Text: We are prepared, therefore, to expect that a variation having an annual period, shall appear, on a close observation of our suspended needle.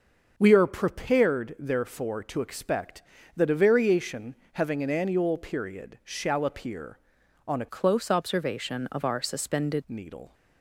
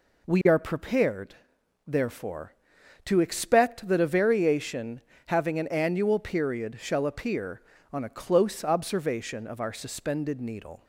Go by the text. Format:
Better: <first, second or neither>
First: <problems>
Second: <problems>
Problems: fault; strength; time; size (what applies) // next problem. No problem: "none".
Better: second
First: starts louder than the rest; until 1.3 s; 6.5 dB // pauses between "variation" and "having"; slight; at 4.3 s; 0.18 s long // changes voice from "close" to "suspended"; from 7.6 to 9.8 s; 2.2 s long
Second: pauses between "variation" and "having"; slight; at 5.0 s; 0.24 s long